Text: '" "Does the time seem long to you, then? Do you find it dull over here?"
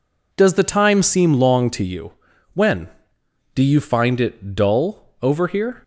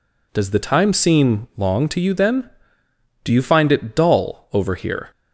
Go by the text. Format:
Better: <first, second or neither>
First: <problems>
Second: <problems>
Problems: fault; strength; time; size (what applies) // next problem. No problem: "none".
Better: second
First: says "when" for "then"; at 2.5 s // pauses between "dull" and "over"; slight; at 5.0 s; 0.16 s long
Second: none